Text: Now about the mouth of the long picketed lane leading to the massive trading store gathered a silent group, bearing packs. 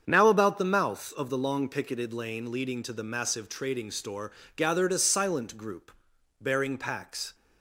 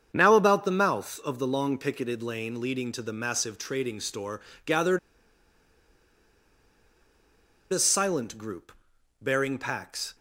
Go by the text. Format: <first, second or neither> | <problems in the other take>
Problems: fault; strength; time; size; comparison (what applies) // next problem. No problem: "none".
first | starts louder than the rest; strong; until 1.1 s; 7.5 dB; strong in the first // pauses between "store" and "gathered"; slight; at 4.4 s; 0.24 s long; slight in the first // pauses between "gathered" and "a"; strong; at 4.9 s; 2.7 s long